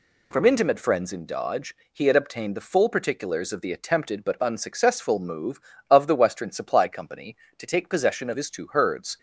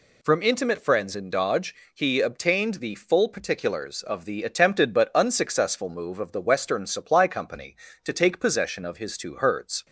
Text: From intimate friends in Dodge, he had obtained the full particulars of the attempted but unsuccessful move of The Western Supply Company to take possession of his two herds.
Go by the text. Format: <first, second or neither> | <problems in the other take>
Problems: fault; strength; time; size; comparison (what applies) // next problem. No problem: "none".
first | skips "had"; at 2.2 s